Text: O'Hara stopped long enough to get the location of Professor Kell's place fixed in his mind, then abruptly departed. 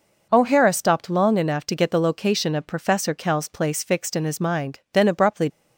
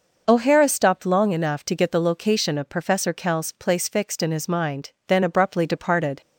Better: second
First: stops before "departed"; at 5.4 s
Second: none

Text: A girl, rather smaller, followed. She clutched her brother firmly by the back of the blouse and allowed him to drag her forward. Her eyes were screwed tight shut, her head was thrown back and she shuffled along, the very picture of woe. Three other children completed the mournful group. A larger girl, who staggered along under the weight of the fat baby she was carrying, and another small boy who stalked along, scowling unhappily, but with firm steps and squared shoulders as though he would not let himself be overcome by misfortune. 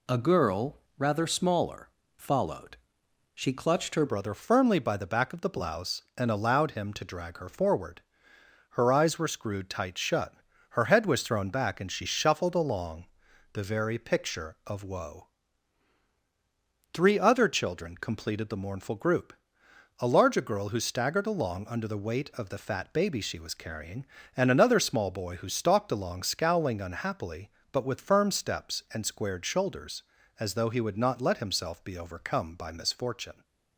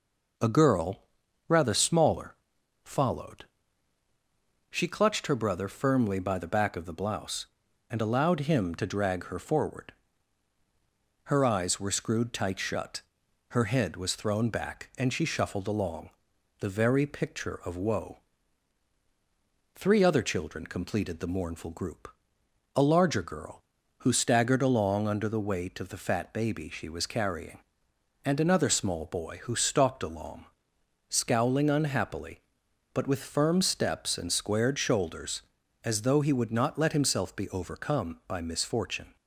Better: second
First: changes voice at "brother"; from 4.0 s on; 29.4 s long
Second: none

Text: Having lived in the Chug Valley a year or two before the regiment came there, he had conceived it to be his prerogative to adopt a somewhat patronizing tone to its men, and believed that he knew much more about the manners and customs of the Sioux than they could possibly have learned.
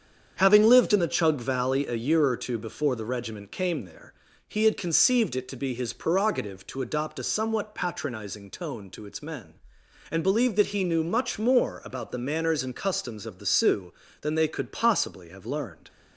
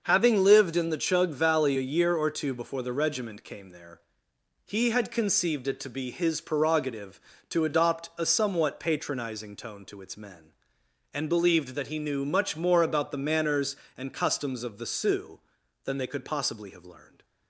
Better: neither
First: starts louder than the rest; strong; until 1.3 s; 7.5 dB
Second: starts louder than the rest; until 1.0 s; 6.5 dB

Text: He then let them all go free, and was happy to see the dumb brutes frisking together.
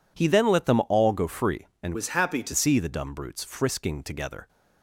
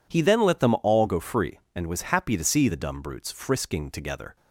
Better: second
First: changes voice from "was" to "to"; from 1.9 to 2.5 s; 0.6 s long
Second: none

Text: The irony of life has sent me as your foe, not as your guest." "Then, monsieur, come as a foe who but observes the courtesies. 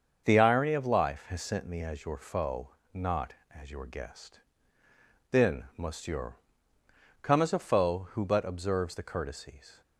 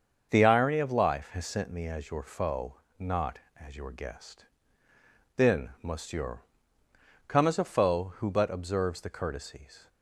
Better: neither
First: starts louder than the rest; until 1.2 s; 6.5 dB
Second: starts louder than the rest; until 1.3 s; 6.5 dB

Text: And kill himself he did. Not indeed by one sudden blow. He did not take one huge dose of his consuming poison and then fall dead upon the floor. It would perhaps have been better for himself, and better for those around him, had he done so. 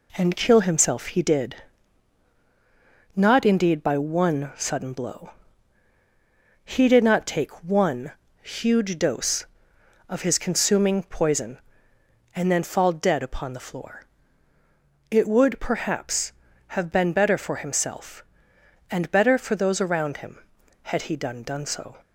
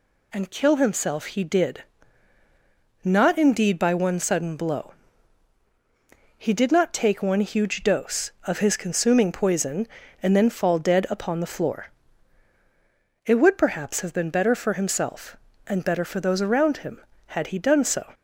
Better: second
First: pauses between "one" and "huge"; slight; at 8.1 s; 0.30 s long // says "done" twice; at 21.4 s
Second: none

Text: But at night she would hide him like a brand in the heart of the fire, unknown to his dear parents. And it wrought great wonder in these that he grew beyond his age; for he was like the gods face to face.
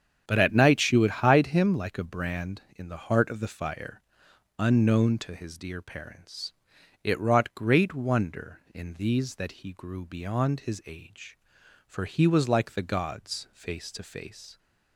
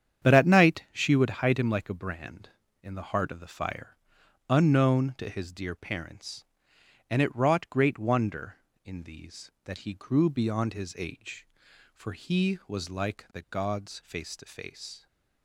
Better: second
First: starts louder than the rest; strong; until 1.3 s; 8.5 dB // skips "And"; at 6.7 s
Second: starts louder than the rest; strong; until 1.3 s; 8.5 dB

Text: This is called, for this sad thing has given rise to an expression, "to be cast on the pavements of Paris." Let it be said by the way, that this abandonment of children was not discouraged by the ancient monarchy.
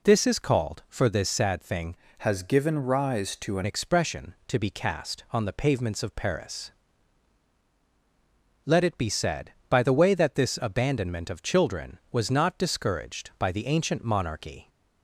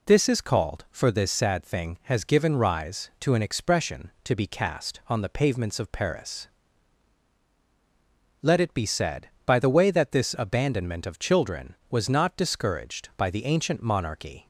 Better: second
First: changes voice from "has" to "an"; from 2.1 to 3.6 s; 1.5 s long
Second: none

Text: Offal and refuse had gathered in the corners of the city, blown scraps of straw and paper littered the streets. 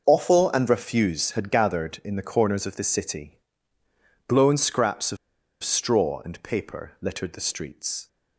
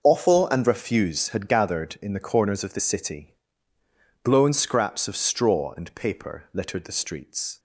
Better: second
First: starts louder than the rest; until 1.0 s; 6 dB // pauses between "of" and "straw"; noticeable; at 5.1 s; 0.46 s long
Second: starts louder than the rest; until 1.0 s; 6 dB

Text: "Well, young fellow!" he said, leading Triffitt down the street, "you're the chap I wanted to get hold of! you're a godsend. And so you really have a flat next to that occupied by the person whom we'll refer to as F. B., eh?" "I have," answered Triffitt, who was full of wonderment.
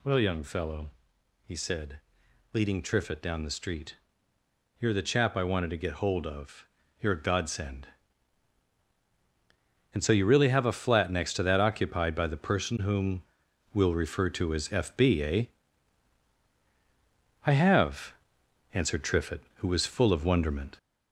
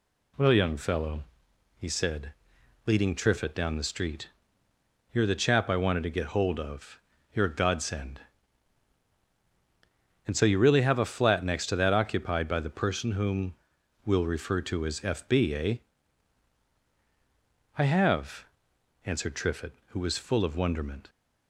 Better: second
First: gets louder; noticeable; throughout; 5.5 dB // pauses between "whom" and "we'll"; noticeable; at 13.2 s; 0.52 s long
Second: pauses between "whom" and "we'll"; noticeable; at 13.5 s; 0.52 s long

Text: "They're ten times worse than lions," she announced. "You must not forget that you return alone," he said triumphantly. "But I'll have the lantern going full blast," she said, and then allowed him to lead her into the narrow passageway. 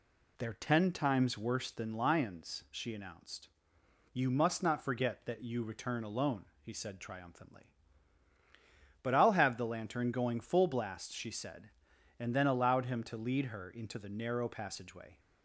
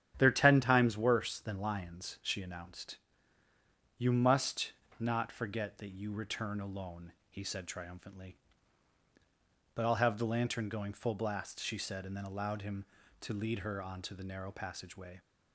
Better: first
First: none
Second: starts louder than the rest; strong; until 1.1 s; 9.5 dB // pauses between "must" and "not"; slight; at 4.7 s; 0.26 s long // says "onto" for "into"; at 13.8 s

